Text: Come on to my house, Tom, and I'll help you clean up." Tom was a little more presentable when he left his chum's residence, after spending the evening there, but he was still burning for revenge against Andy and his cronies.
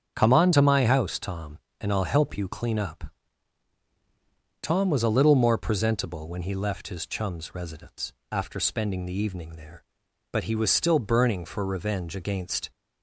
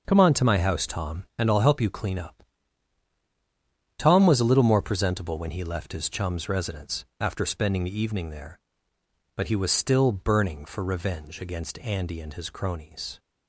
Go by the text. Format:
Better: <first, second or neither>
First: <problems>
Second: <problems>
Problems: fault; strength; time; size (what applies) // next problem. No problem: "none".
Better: second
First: starts louder than the rest; strong; until 1.1 s; 7.5 dB // stops before "Andy and his cronies"; at 12.7 s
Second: starts louder than the rest; noticeable; until 1.0 s; 6 dB